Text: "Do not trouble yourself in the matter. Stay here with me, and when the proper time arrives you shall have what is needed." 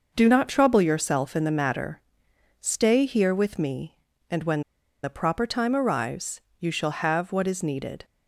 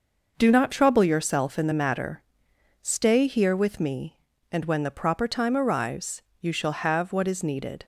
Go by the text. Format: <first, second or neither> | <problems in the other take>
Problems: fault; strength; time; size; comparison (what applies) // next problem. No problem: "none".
second | pauses between "when" and "the"; at 4.6 s; 0.43 s long // pauses between "arrives" and "you"; slight; at 6.4 s; 0.18 s long; slight in the second